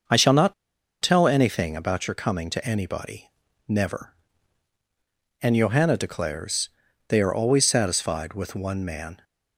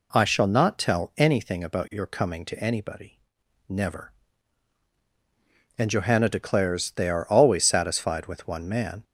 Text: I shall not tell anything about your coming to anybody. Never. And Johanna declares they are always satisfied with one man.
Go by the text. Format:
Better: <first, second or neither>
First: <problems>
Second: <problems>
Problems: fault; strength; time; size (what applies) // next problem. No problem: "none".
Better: second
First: starts louder than the rest; until 1.5 s; 6.5 dB // pauses between "not" and "tell"; noticeable; at 0.5 s; 0.48 s long // pauses between "declares" and "they"; at 6.6 s; 0.38 s long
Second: none